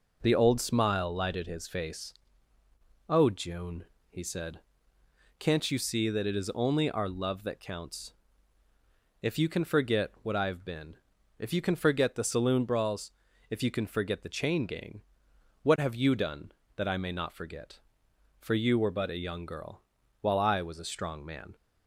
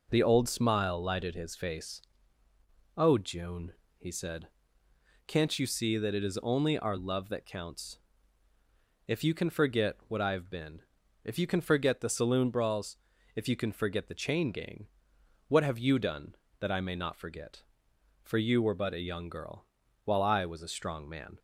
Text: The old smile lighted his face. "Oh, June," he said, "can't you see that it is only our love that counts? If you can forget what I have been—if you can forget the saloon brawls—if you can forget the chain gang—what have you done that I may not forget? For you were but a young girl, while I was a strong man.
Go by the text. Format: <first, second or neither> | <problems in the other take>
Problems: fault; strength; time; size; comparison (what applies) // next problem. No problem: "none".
neither | none